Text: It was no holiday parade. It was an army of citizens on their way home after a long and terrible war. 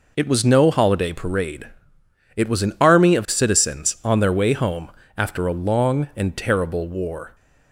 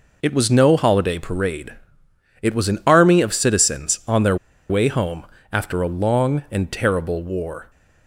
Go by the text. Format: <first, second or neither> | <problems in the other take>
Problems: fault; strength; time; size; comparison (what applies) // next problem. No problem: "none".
first | pauses between "their" and "way"; slight; at 4.3 s; 0.33 s long // pauses between "home" and "after"; slight; at 5.2 s; 0.26 s long; slight in the first